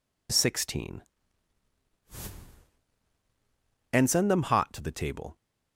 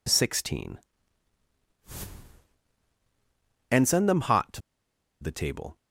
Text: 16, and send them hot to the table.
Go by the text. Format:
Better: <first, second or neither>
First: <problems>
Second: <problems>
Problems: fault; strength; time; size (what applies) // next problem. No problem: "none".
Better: first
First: none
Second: pauses between "to" and "the"; noticeable; at 4.6 s; 0.60 s long